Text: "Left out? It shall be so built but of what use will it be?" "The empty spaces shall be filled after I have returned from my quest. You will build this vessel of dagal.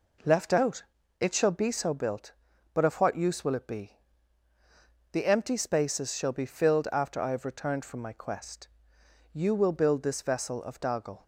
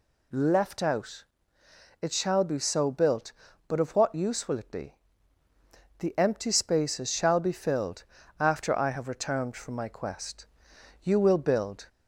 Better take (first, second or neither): first